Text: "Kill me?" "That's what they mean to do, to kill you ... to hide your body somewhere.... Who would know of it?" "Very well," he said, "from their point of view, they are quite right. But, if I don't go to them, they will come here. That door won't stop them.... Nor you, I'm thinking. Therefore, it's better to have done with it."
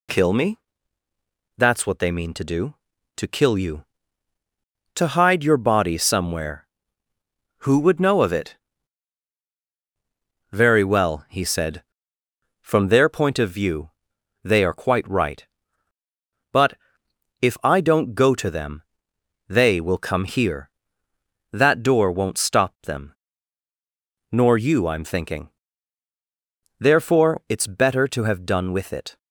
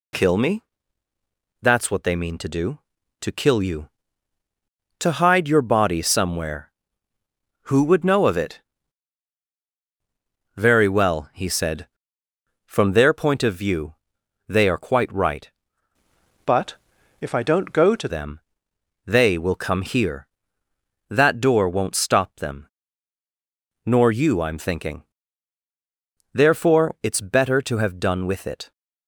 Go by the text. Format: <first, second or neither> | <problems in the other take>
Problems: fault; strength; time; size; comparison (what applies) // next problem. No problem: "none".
first | changes voice from "But" to "to"; from 16.4 to 18.0 s; 1.6 s long